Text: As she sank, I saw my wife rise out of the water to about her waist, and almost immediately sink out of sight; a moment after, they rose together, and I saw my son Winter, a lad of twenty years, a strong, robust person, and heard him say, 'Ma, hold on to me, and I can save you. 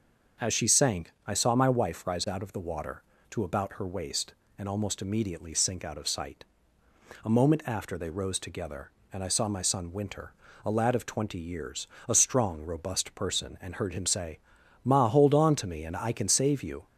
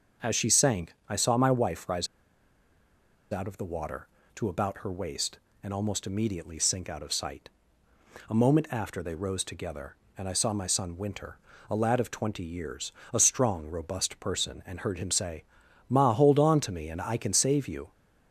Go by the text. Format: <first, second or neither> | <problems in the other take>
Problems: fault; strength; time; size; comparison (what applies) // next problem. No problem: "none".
first | starts louder than the rest; until 1.3 s; 6.5 dB; also in the first // pauses between "rise" and "out"; strong; at 2.0 s; 1.2 s long